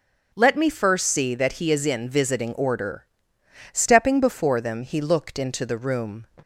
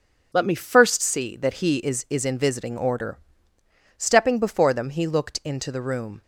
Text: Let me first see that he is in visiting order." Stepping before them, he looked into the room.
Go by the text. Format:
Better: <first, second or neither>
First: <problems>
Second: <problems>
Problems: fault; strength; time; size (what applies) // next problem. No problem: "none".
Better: first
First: starts louder than the rest; noticeable; until 1.3 s; 6 dB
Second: starts louder than the rest; noticeable; until 1.3 s; 6 dB // says "is" twice; at 2.0 s